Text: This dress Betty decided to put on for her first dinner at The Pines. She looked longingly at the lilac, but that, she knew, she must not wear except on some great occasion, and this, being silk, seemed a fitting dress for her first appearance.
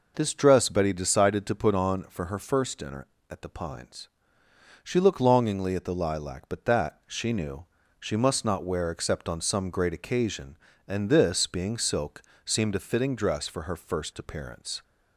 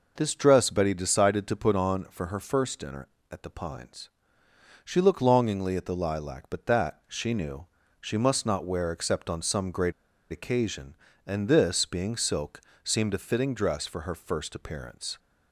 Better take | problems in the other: first | pauses between "great" and "occasion"; at 9.9 s; 0.37 s long

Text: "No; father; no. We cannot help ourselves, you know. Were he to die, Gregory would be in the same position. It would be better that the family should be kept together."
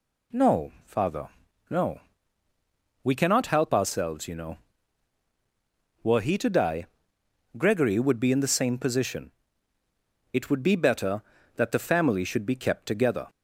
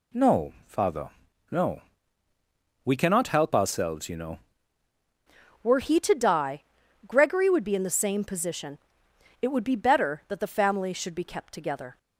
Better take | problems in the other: first | changes voice at "Were"; from 5.6 s on; 6.3 s long

